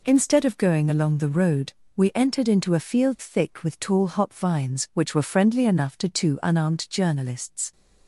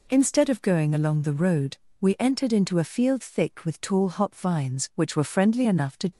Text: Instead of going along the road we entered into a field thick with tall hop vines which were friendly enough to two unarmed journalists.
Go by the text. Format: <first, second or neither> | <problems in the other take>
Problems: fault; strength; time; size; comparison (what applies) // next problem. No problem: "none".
first | pauses between "road" and "we"; slight; at 1.7 s; 0.22 s long; slight in the first // stops before "two unarmed journalists"; at 6.1 s